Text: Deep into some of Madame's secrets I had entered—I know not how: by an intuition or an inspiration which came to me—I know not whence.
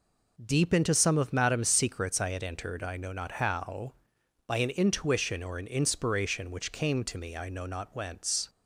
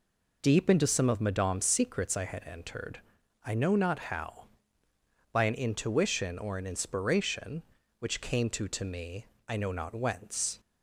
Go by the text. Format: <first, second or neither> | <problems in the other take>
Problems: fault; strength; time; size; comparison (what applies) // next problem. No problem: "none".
first | says "to" twice; at 8.6 s